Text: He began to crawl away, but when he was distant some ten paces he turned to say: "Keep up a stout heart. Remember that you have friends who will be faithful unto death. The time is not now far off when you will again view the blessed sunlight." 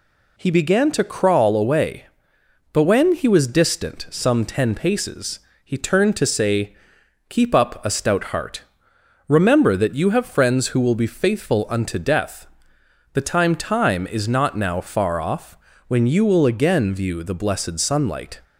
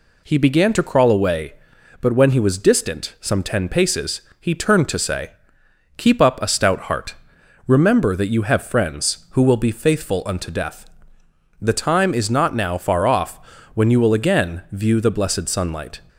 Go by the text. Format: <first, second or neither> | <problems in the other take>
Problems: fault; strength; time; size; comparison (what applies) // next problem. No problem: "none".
second | pauses between "paces" and "he"; slight; at 5.3 s; 0.24 s long; slight in the second // says "time" twice; at 13.5 s // pauses between "off" and "when"; slight; at 15.5 s; 0.32 s long; slight in the second